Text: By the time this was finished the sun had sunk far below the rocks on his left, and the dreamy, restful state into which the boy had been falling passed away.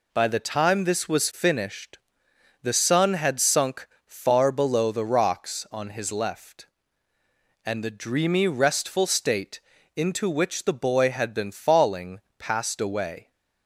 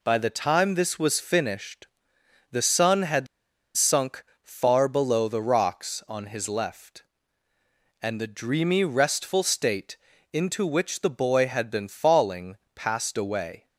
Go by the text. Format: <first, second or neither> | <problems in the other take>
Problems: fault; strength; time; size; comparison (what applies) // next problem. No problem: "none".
first | pauses between "finished" and "the"; noticeable; at 1.8 s; 0.66 s long; noticeable in the first // pauses between "had" and "sunk"; noticeable; at 3.2 s; 0.50 s long // pauses between "sunk" and "far"; slight; at 4.2 s; 0.20 s long; slight in the first // pauses between "state" and "into"; at 9.9 s; 0.38 s long; also in the first // pauses between "falling" and "passed"; slight; at 12.5 s; 0.18 s long; slight in the first